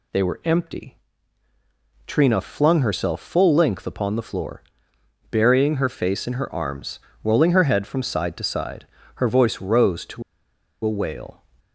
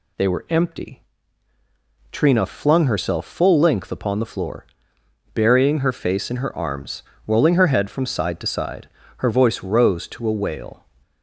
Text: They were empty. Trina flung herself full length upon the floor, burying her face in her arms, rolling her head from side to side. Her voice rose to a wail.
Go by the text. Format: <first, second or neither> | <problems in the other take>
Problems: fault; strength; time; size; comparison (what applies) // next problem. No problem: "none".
second | pauses between "to" and "a"; noticeable; at 10.2 s; 0.62 s long